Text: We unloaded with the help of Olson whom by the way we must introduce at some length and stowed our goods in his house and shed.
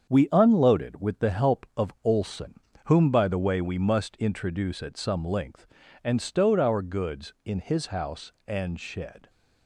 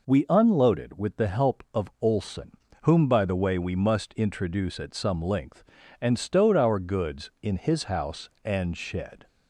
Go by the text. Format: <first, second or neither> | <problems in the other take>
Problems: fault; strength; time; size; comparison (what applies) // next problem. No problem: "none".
second | gets quieter; strong; throughout; 7.5 dB // pauses between "Olson" and "whom"; slight; at 2.5 s; 0.32 s long; slight in the second